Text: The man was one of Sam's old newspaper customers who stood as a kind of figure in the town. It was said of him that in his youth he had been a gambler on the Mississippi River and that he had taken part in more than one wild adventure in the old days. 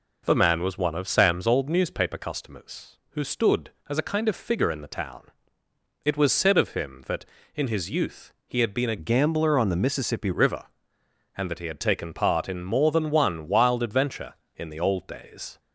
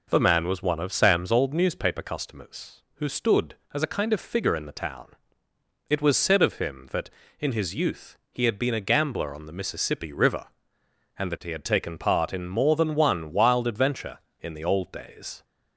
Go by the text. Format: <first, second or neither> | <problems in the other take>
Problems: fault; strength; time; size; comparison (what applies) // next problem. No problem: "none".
second | pauses between "youth" and "he"; slight; at 8.3 s; 0.16 s long; slight in the second // changes voice from "gambler" to "Mississippi"; from 8.9 to 10.3 s; 1.4 s long